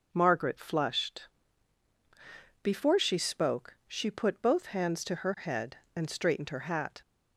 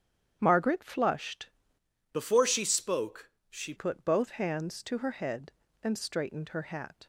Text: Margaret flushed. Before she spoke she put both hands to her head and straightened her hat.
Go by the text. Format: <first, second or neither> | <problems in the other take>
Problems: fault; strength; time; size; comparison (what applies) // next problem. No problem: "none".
first | starts louder than the rest; strong; until 1.4 s; 9 dB; also in the first // changes voice from "Before" to "she"; from 2.1 to 3.7 s; 1.6 s long // pauses between "spoke" and "she"; slight; at 3.2 s; 0.22 s long